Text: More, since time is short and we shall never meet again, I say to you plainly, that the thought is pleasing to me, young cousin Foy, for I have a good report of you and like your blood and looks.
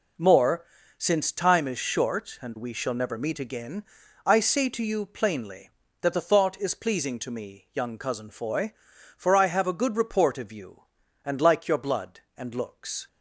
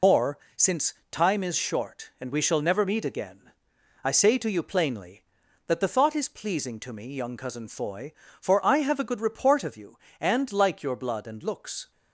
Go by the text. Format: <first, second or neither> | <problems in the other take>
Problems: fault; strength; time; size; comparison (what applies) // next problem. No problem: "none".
first | loses the start of "More"; at 0.0 s; 80 ms // pauses between "since" and "time"; slight; at 0.9 s; 0.16 s long